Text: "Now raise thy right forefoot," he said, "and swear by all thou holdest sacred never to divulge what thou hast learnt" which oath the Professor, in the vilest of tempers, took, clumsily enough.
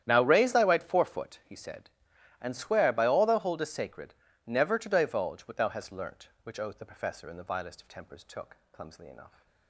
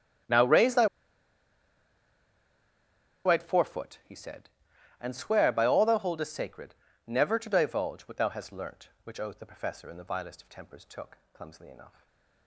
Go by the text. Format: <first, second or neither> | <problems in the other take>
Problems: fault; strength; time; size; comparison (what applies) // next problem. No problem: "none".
first | starts louder than the rest; strong; until 3.6 s; 10.5 dB; strong in the first // pauses between "thy" and "right"; strong; at 0.8 s; 2.4 s long // pauses between "sacred" and "never"; slight; at 6.7 s; 0.34 s long; slight in the first // stays silent after the last word; slight; from 11.8 s on; 0.6 s long